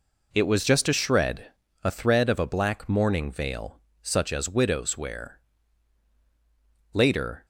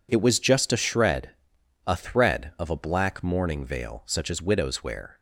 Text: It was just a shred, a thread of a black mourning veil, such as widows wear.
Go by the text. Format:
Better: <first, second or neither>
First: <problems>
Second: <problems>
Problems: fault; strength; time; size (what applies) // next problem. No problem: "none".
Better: second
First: goes on to say "Later"; from 6.9 s on; 0.52 s long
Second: none